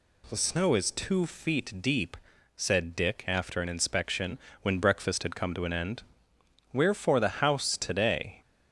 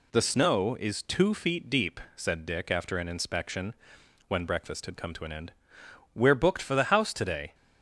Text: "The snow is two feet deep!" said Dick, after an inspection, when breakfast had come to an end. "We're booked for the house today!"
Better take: second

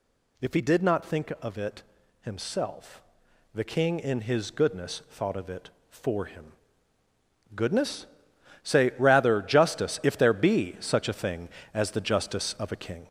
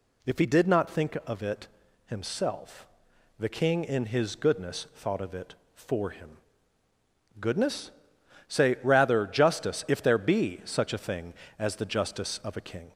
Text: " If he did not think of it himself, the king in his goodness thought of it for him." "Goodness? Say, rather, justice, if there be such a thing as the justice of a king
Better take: second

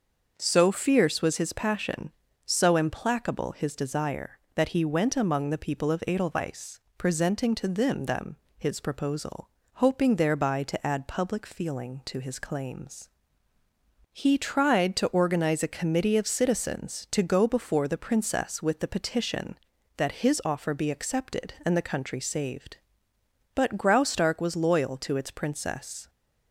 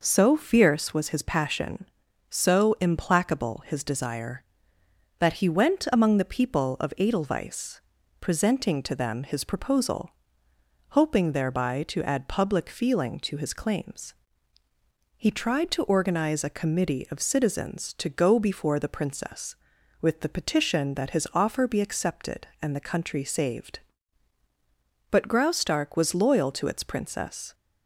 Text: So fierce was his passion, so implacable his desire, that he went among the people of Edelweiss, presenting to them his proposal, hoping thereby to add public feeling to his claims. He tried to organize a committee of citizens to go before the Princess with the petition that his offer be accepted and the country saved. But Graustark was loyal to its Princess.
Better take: second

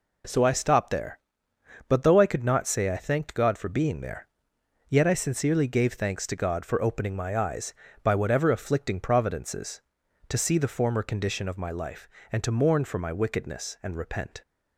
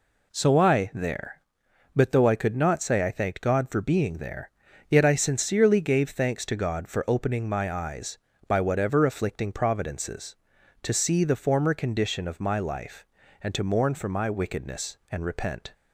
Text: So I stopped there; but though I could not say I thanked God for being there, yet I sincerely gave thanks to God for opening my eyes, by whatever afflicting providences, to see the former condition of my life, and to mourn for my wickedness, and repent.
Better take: first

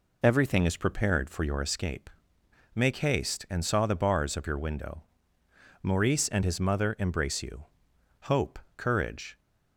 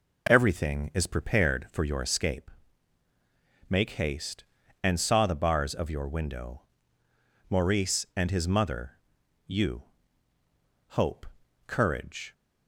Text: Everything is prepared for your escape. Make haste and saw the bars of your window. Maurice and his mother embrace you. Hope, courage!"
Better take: first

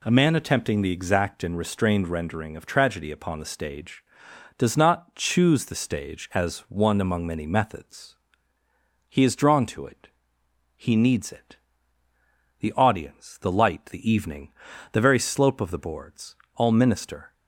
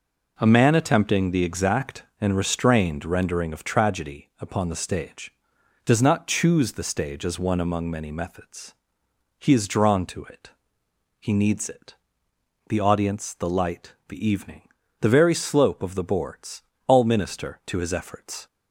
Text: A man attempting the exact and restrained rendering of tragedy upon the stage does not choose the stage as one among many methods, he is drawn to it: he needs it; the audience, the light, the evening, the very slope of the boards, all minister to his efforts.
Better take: second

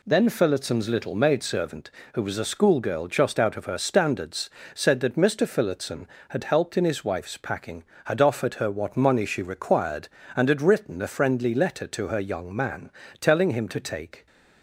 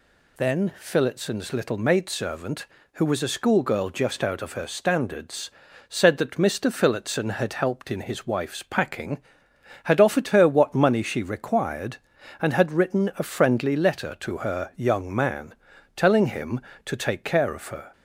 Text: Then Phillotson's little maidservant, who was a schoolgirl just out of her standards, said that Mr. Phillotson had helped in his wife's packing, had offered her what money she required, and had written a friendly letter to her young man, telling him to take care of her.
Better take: second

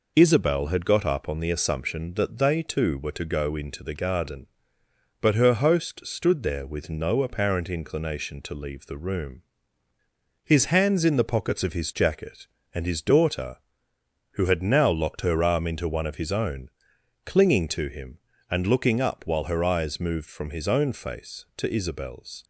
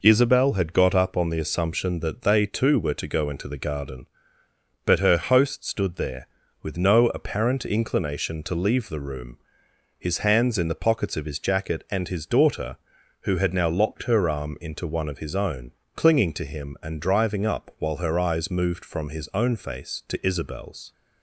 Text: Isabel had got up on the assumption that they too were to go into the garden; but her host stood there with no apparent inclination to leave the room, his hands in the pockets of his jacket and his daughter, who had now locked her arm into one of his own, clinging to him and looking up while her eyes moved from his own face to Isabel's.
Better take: first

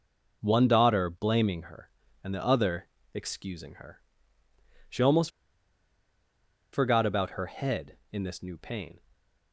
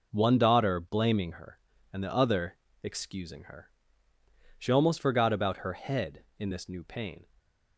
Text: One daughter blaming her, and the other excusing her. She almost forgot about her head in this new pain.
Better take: second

